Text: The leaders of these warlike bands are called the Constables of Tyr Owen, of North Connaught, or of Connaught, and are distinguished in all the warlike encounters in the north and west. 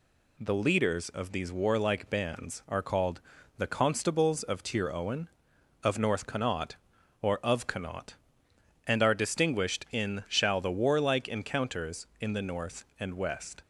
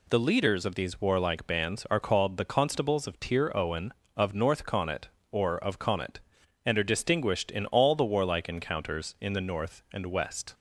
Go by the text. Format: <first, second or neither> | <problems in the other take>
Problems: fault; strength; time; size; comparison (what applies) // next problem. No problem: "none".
second | pauses between "called" and "the"; slight; at 3.2 s; 0.36 s long // says "shall" for "all"; at 10.2 s